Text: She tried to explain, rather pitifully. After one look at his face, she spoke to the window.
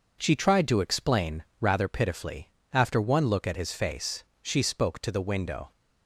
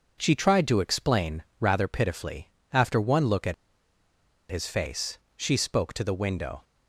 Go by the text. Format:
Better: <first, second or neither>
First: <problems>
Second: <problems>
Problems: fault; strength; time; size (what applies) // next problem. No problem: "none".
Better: first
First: none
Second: pauses between "at" and "his"; noticeable; at 3.5 s; 0.95 s long